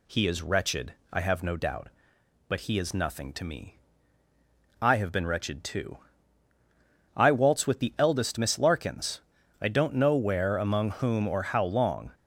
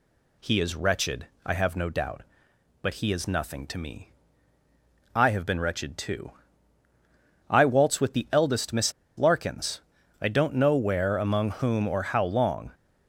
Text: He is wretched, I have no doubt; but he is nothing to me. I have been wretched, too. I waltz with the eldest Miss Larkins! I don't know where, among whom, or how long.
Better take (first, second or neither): first